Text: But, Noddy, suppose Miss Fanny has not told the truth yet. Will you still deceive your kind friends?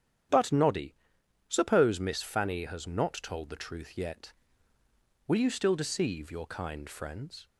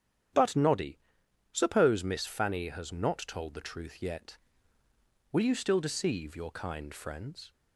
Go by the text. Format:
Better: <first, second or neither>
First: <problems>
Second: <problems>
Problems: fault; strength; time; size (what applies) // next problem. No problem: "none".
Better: neither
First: starts louder than the rest; strong; until 1.8 s; 9.5 dB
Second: starts louder than the rest; strong; until 1.8 s; 9.5 dB